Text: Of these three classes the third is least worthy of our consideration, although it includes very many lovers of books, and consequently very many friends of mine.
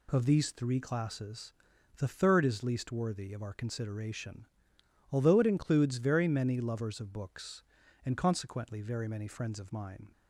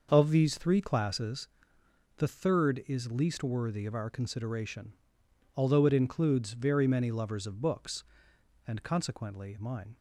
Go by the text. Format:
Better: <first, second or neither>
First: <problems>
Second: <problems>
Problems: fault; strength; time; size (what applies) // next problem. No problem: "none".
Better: first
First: pauses between "classes" and "the"; noticeable; at 1.5 s; 0.46 s long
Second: pauses between "classes" and "the"; noticeable; at 1.4 s; 0.68 s long // skips "very many friends of"; at 9.5 s